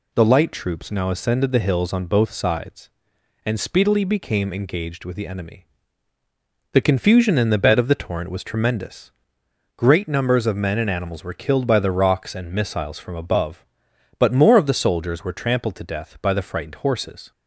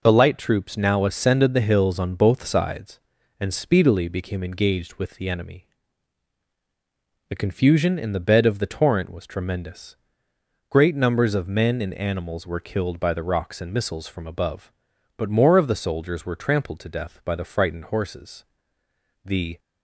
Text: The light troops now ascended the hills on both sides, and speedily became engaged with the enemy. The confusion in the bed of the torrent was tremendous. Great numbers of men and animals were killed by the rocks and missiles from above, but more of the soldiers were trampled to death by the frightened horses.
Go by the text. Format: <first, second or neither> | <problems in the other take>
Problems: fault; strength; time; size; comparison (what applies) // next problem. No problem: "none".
first | goes on to say "The"; slight; from 19.2 s on; 0.34 s long